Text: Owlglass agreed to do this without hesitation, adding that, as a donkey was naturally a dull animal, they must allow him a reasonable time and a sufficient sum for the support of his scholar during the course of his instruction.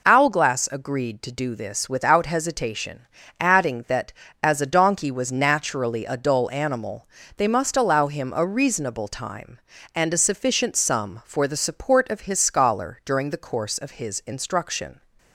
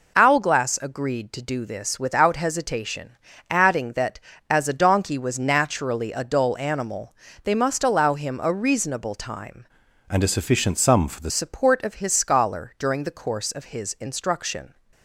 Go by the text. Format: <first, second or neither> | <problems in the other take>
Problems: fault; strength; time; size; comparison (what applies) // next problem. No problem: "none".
first | changes voice from "and" to "the"; from 10.0 to 11.3 s; 1.3 s long